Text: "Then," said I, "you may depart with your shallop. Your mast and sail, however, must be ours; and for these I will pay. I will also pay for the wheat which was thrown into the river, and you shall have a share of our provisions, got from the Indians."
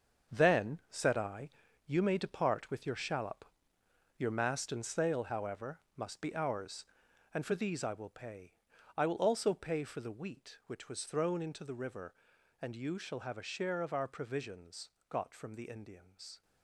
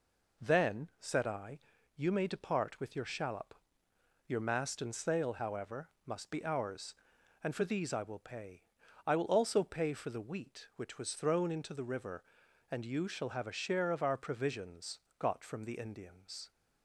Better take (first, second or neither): second